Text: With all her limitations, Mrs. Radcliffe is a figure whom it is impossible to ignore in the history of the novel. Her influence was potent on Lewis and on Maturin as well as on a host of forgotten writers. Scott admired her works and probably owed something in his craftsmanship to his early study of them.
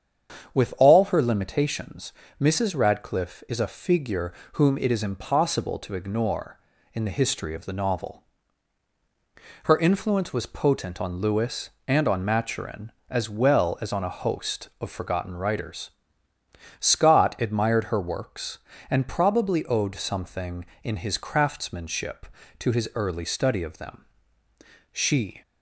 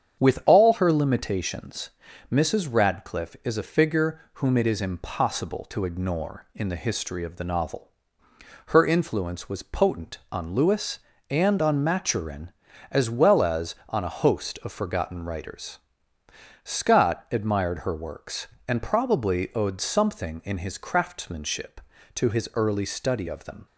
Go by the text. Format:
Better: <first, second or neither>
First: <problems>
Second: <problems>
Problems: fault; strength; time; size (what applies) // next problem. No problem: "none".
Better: second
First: starts louder than the rest; strong; until 1.5 s; 7.5 dB // pauses between "figure" and "whom"; slight; at 4.3 s; 0.20 s long // goes on to say "She"; from 24.9 s on; 0.50 s long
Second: starts louder than the rest; strong; until 1.2 s; 8 dB